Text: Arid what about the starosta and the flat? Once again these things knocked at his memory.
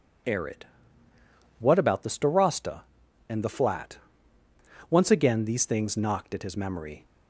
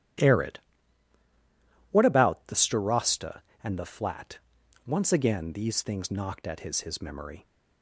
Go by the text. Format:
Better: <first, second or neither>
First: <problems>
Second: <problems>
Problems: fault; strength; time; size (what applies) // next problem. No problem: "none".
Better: first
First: pauses between "Arid" and "what"; noticeable; at 0.6 s; 0.94 s long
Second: starts louder than the rest; strong; until 2.5 s; 12 dB // pauses between "Arid" and "what"; strong; at 0.5 s; 1.3 s long // says "his" twice; at 6.8 s